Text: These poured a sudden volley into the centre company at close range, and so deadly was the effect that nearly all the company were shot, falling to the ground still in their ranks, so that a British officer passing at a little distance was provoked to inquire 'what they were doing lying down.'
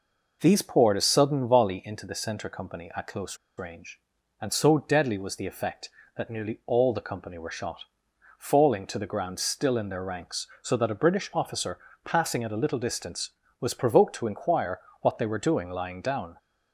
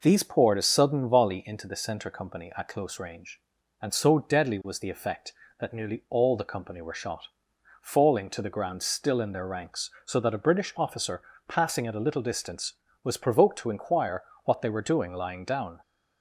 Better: second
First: pauses between "close" and "range"; slight; at 3.3 s; 0.21 s long // pauses between "officer" and "passing"; slight; at 11.7 s; 0.28 s long // pauses between "inquire" and "what"; slight; at 14.8 s; 0.20 s long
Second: pauses between "officer" and "passing"; slight; at 11.1 s; 0.28 s long // pauses between "inquire" and "what"; slight; at 14.2 s; 0.20 s long

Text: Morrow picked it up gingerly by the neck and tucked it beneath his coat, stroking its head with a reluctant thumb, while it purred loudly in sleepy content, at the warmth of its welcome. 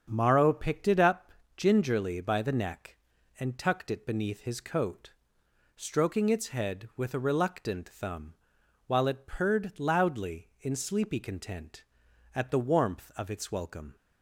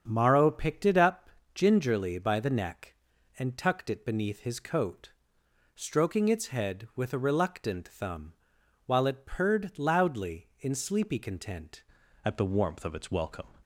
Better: first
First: starts louder than the rest; strong; until 1.1 s; 7 dB // pauses between "up" and "gingerly"; slight; at 1.3 s; 0.22 s long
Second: starts louder than the rest; strong; until 1.0 s; 7 dB // pauses between "up" and "gingerly"; slight; at 1.3 s; 0.22 s long // changes voice at "at"; from 12.2 s on; 1.2 s long

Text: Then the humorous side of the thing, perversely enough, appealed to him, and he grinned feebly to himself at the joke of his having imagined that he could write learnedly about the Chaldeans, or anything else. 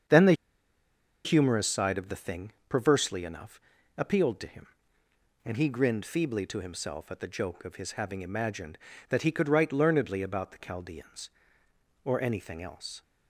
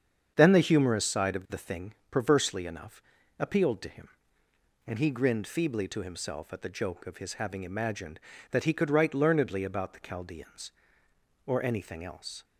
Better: second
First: starts louder than the rest; strong; until 2.0 s; 7.5 dB // pauses between "the" and "humorous"; noticeable; at 0.3 s; 0.91 s long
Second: starts louder than the rest; strong; until 1.3 s; 7.5 dB

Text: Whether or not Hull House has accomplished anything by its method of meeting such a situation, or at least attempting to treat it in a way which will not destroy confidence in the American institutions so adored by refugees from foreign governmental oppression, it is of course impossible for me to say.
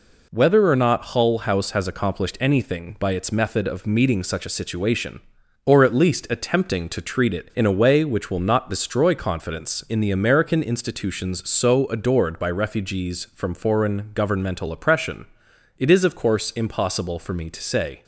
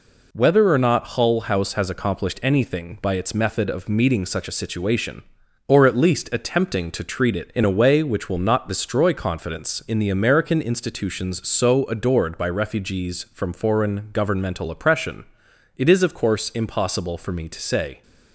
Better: neither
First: none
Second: none

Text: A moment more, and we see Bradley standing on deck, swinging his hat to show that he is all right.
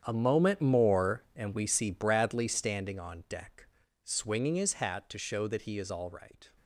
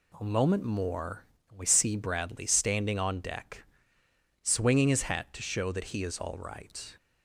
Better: second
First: gets quieter; strong; throughout; 14 dB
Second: none

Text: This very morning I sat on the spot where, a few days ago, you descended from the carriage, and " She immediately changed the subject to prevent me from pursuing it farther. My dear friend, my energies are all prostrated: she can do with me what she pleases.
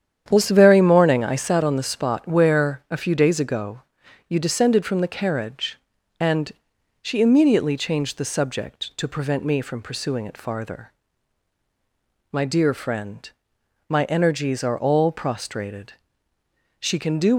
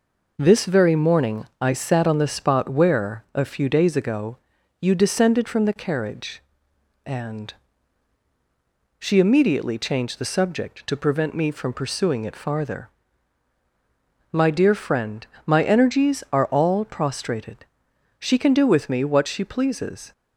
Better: second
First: starts louder than the rest; strong; until 1.2 s; 9 dB // stops before "with me what she pleases"; at 17.3 s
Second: none

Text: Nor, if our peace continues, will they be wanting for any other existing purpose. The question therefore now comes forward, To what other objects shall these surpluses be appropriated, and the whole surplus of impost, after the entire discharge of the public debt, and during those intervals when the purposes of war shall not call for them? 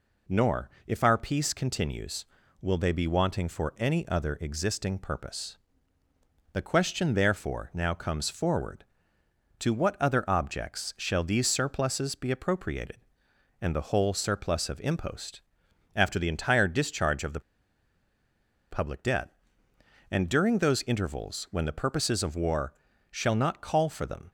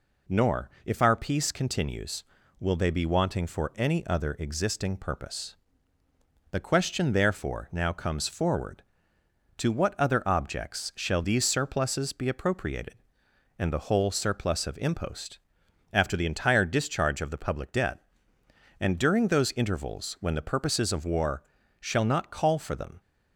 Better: second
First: pauses between "the" and "public"; strong; at 17.4 s; 1.3 s long // pauses between "war" and "shall"; at 22.7 s; 0.38 s long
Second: pauses between "war" and "shall"; at 21.4 s; 0.38 s long

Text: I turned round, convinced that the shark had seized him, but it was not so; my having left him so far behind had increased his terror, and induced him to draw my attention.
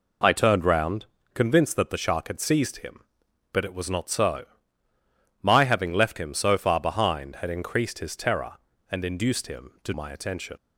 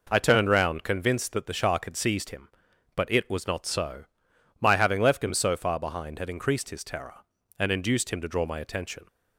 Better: second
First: skips "draw"; at 9.9 s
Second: none

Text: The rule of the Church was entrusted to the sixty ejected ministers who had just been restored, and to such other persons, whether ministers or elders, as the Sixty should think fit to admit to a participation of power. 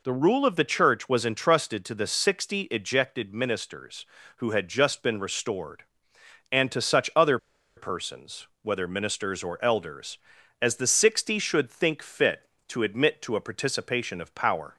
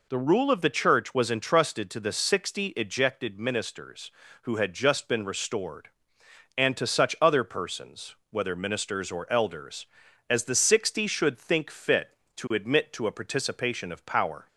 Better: second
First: pauses between "other" and "persons"; at 7.3 s; 0.39 s long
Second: none

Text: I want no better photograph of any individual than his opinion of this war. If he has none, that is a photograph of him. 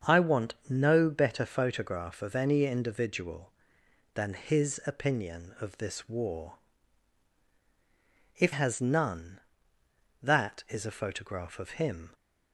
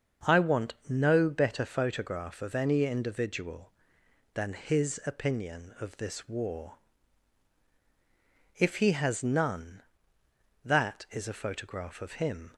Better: second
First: starts louder than the rest; until 1.1 s; 7 dB // skips "he"; at 8.5 s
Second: starts louder than the rest; until 1.3 s; 6.5 dB

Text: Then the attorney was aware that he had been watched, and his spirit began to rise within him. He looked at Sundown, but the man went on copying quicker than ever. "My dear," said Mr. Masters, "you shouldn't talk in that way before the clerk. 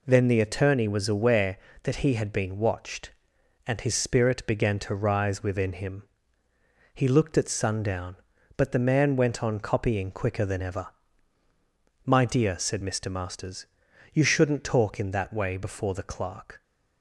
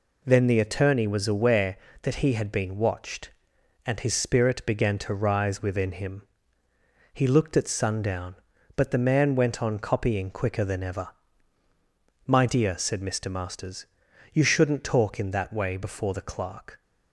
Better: neither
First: none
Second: none

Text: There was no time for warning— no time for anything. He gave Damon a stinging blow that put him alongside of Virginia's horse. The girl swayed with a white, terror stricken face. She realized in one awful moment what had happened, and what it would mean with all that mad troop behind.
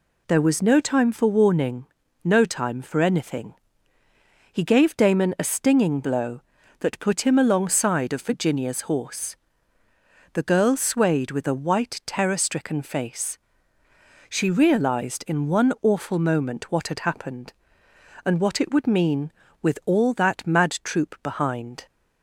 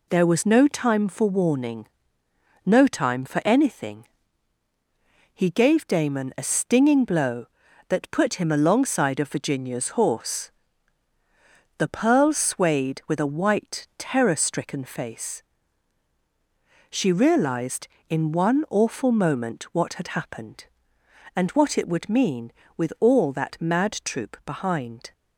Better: first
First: none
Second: says "pearl" for "girl"; at 11.8 s

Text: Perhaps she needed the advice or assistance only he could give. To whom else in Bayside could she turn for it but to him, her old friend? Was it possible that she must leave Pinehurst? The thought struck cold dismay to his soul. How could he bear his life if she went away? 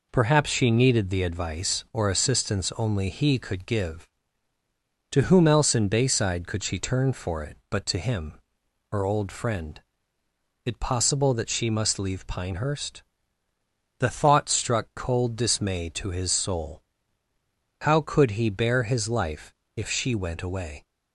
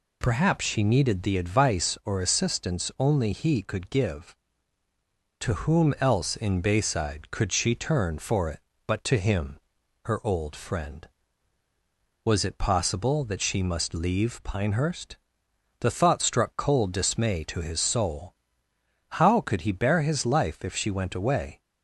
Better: second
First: skips "Was"; at 10.2 s // pauses between "life" and "if"; slight; at 19.5 s; 0.20 s long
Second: none

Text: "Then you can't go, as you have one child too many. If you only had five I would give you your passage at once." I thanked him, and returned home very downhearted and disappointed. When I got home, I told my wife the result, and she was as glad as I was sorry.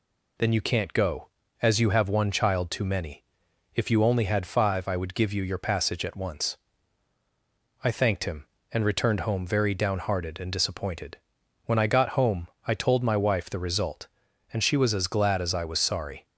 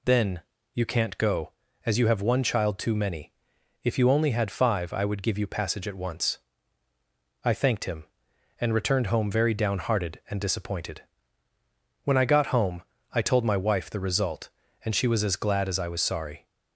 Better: first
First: none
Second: pauses between "Then" and "you"; slight; at 0.4 s; 0.32 s long // skips "your"; at 5.4 s

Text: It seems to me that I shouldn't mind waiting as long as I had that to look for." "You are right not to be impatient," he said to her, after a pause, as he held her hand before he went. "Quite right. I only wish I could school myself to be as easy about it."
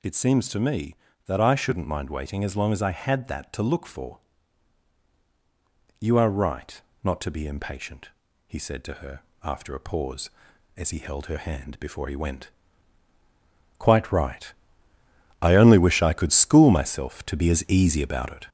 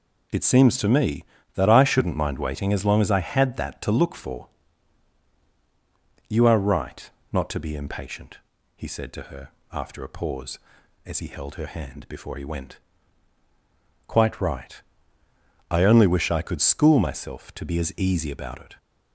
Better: second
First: gets louder; throughout; 4 dB // pauses between "right" and "not"; slight; at 6.8 s; 0.22 s long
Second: pauses between "right" and "not"; slight; at 7.0 s; 0.22 s long

